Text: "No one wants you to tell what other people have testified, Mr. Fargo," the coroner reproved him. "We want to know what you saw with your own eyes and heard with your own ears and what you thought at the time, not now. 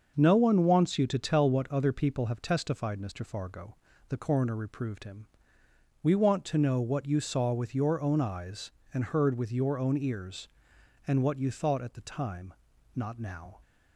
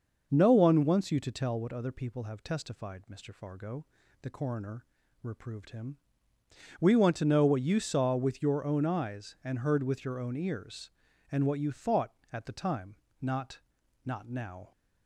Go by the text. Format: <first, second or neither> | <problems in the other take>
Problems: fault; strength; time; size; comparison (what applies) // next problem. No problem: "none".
first | starts louder than the rest; noticeable; until 1.3 s; 6 dB; also in the first // pauses between "coroner" and "reproved"; at 4.8 s; 0.38 s long // says "not" twice; at 14.0 s